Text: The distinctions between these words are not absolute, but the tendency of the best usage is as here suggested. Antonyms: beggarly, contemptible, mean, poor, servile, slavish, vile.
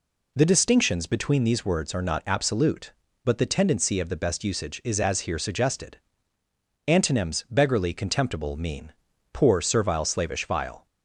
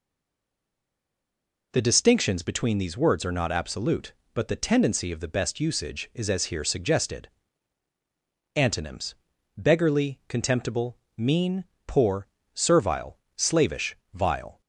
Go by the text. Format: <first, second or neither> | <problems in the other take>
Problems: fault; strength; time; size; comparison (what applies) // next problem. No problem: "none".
first | stays silent before the first word; noticeable; until 1.7 s; 1.7 s long